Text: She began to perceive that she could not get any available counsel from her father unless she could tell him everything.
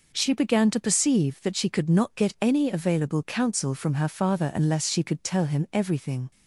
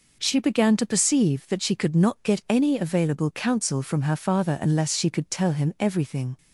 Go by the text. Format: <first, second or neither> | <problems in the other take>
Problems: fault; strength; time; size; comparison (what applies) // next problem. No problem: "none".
neither | none